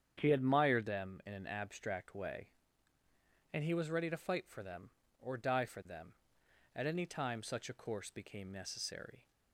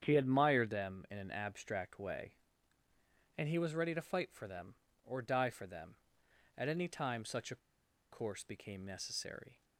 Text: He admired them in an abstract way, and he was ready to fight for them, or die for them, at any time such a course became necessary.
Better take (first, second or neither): first